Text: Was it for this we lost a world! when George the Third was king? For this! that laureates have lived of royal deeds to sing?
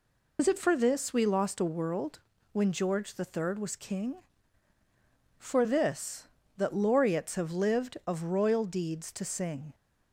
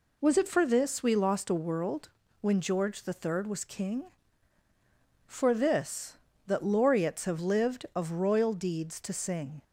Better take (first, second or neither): second